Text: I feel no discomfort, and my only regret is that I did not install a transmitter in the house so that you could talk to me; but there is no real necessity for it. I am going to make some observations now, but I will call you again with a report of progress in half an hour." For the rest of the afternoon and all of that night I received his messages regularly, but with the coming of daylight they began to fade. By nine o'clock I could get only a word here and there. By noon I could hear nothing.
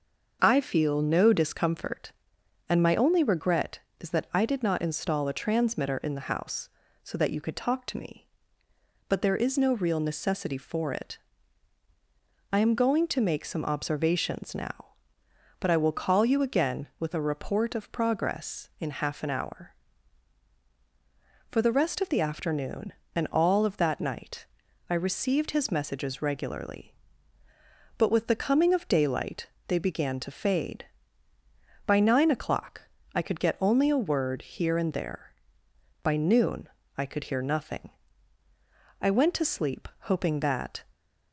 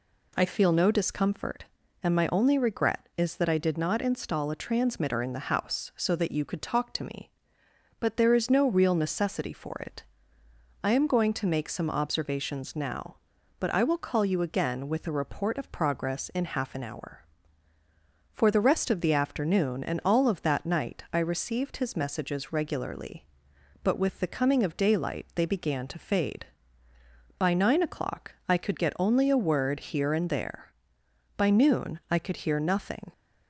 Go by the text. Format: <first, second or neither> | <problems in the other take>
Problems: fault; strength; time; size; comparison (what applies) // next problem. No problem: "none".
second | starts louder than the rest; until 1.4 s; 6.5 dB // pauses between "night" and "I"; at 24.4 s; 0.44 s long // pauses between "daylight" and "they"; slight; at 29.4 s; 0.18 s long // pauses between "o'clock" and "I"; slight; at 32.8 s; 0.32 s long // pauses between "noon" and "I"; slight; at 36.6 s; 0.30 s long // goes on to say "I went to sleep hoping that"; strong; from 39.0 s on; 1.8 s long